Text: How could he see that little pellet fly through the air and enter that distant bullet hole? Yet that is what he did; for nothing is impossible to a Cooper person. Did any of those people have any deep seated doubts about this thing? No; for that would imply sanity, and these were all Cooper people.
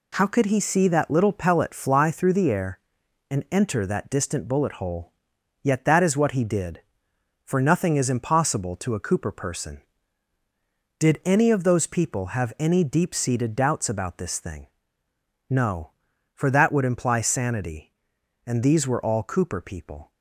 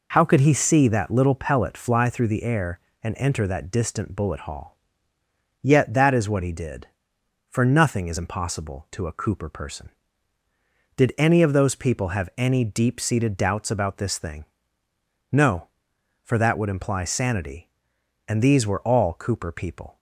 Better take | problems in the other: first | says "hall" for "hole"; at 4.4 s

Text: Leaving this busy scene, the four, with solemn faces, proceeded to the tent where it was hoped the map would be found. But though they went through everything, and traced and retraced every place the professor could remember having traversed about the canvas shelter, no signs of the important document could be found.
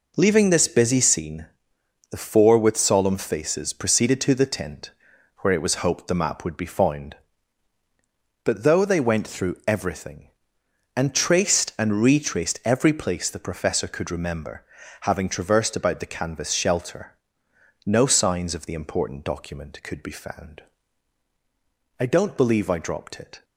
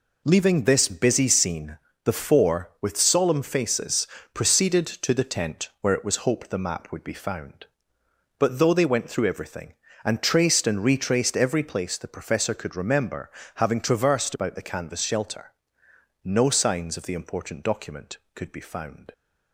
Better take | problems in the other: second | pauses between "tent" and "where"; noticeable; at 4.9 s; 0.46 s long // pauses between "remember" and "having"; at 14.6 s; 0.38 s long; slight in the second // goes on to say "I don't believe I dropped it"; from 21.9 s on; 1.4 s long

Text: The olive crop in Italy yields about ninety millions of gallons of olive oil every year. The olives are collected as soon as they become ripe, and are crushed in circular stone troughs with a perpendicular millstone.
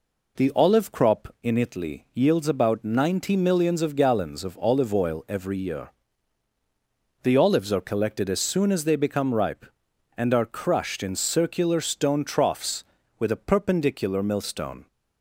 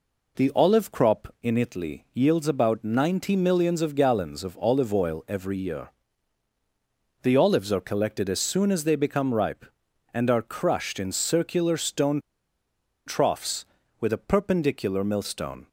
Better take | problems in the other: first | pauses between "stone" and "troughs"; noticeable; at 12.2 s; 0.85 s long

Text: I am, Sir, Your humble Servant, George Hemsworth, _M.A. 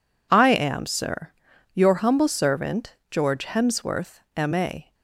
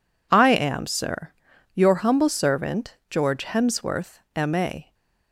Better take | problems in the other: neither | none

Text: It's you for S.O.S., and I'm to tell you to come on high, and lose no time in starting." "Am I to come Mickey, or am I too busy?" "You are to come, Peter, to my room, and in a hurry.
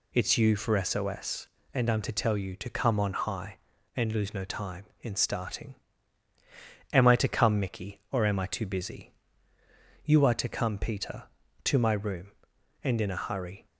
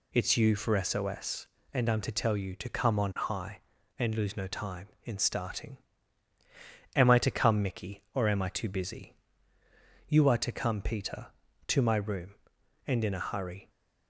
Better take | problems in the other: neither | none

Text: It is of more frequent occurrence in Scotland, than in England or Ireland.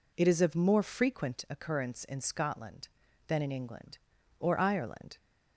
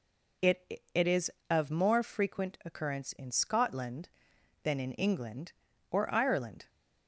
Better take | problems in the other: first | says "It" twice; at 0.9 s

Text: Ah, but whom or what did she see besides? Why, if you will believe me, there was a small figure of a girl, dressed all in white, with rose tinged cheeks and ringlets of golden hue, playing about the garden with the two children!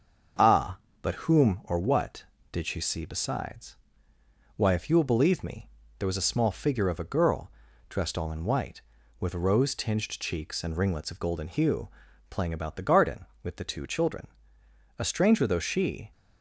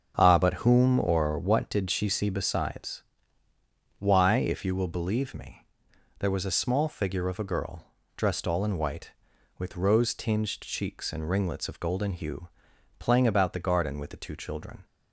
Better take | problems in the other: second | starts louder than the rest; until 1.6 s; 7 dB; strong in the second // goes on to say "A stranger though she"; noticeable; from 14.9 s on; 1.1 s long

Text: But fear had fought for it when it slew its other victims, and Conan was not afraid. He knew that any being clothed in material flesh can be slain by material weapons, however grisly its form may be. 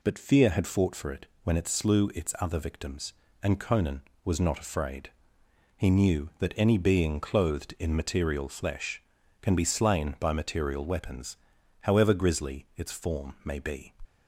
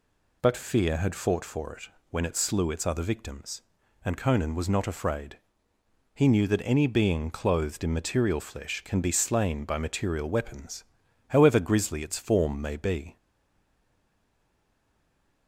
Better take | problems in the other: first | pauses between "it" and "when"; slight; at 1.8 s; 0.20 s long; slight in the first // stays silent after the last word; from 13.1 s on; 2.3 s long

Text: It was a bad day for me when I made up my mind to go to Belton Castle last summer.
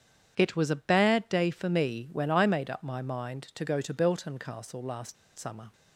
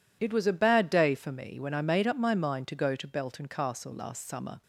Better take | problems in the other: second | starts louder than the rest; strong; until 1.3 s; 8.5 dB // pauses between "last" and "summer"; slight; at 5.1 s; 0.23 s long

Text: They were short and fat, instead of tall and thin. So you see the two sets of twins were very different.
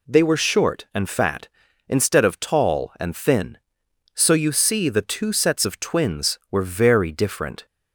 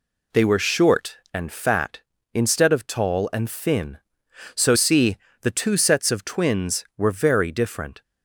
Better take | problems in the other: first | skips "you"; at 4.7 s // pauses between "see" and "the"; slight; at 5.1 s; 0.24 s long

